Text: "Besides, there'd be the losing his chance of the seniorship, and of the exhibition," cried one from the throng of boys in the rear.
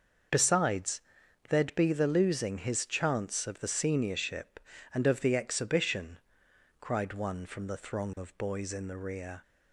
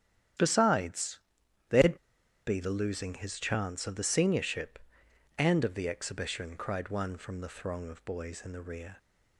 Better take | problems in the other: first | starts louder than the rest; strong; until 1.9 s; 10 dB; also in the first // pauses between "there'd" and "be"; noticeable; at 1.9 s; 0.50 s long

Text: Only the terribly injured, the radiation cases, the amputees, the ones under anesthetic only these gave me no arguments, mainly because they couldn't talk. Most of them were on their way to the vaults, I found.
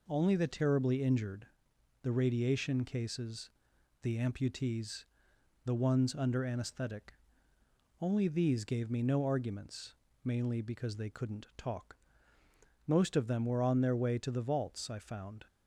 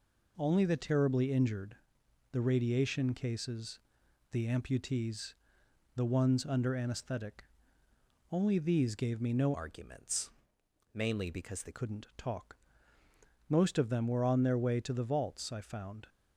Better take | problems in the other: first | pauses between "anesthetic" and "only"; noticeable; at 7.4 s; 0.88 s long; noticeable in the first // changes voice from "arguments" to "they"; from 9.5 to 11.7 s; 2.2 s long

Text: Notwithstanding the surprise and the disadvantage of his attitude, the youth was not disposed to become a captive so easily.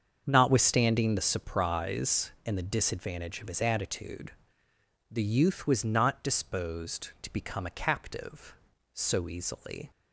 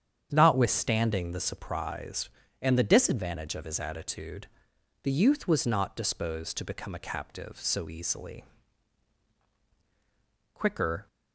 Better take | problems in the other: first | starts louder than the rest; strong; until 1.3 s; 8.5 dB; strong in the first // goes on to say "Quicker"; from 10.5 s on; 0.54 s long

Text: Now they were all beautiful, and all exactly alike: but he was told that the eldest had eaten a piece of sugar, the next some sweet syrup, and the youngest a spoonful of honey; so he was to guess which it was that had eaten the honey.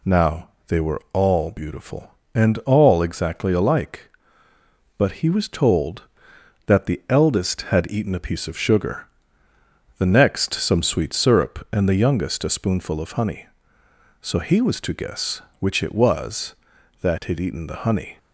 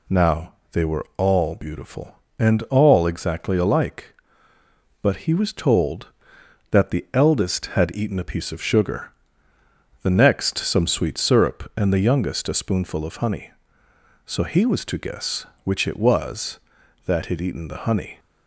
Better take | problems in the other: neither | pauses between "Now" and "they"; slight; the same in both

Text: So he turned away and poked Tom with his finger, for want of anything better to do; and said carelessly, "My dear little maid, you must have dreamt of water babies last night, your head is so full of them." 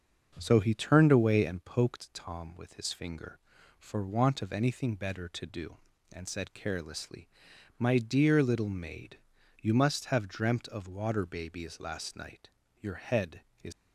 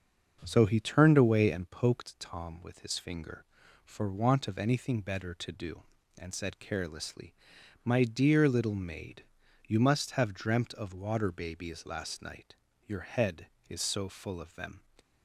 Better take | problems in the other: second | starts louder than the rest; until 1.4 s; 7 dB; also in the second // stops before "so full of them"; at 13.7 s

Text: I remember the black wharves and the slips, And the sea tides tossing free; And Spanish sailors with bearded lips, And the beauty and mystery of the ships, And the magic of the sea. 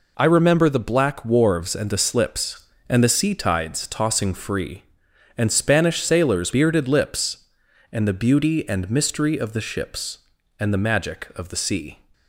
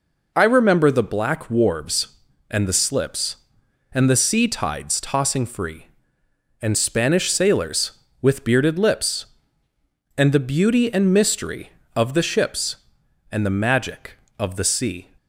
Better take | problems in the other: second | skips "with"; at 6.5 s

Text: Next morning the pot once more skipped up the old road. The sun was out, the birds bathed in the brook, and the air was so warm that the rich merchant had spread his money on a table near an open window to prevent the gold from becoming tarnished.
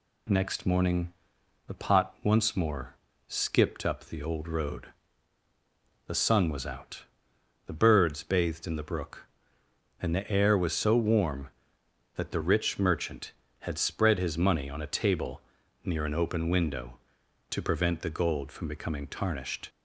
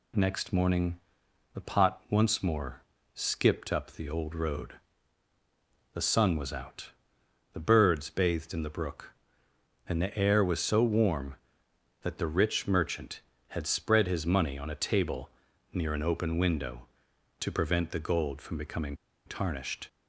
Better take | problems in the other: first | pauses between "morning" and "the"; noticeable; at 1.0 s; 0.54 s long; noticeable in the first // pauses between "more" and "skipped"; slight; at 2.8 s; 0.32 s long; slight in the first // pauses between "table" and "near"; at 15.3 s; 0.42 s long; also in the first // pauses between "becoming" and "tarnished"; slight; at 18.9 s; 0.31 s long

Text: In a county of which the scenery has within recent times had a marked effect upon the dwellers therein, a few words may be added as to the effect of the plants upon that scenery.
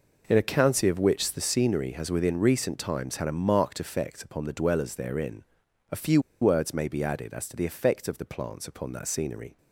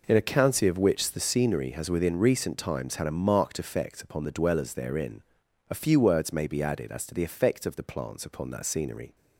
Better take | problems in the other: second | pauses between "few" and "words"; slight; at 6.1 s; 0.21 s long

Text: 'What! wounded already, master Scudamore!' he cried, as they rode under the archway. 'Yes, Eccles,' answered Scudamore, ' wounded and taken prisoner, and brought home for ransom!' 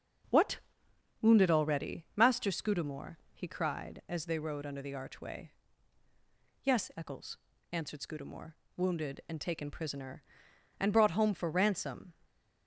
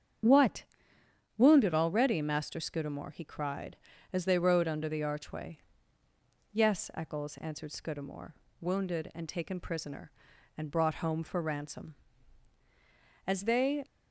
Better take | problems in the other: first | starts louder than the rest; strong; until 1.9 s; 7.5 dB; also in the first // goes on to say "As they"; from 13.2 s on; 0.58 s long

